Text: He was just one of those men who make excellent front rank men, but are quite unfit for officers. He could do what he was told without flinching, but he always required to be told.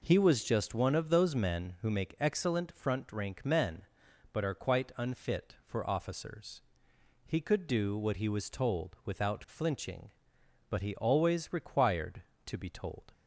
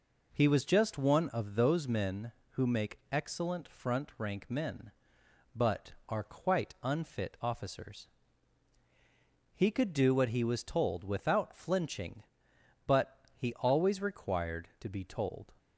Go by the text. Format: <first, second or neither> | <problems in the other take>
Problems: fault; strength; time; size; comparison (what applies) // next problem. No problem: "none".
first | skips "for"; at 7.3 s // pauses between "but" and "he"; slight; at 13.1 s; 0.18 s long